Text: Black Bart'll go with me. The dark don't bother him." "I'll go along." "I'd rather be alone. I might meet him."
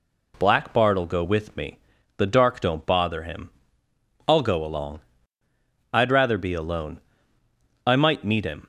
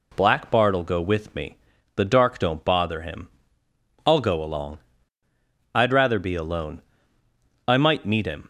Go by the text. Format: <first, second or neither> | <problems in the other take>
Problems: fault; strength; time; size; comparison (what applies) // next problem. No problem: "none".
neither | none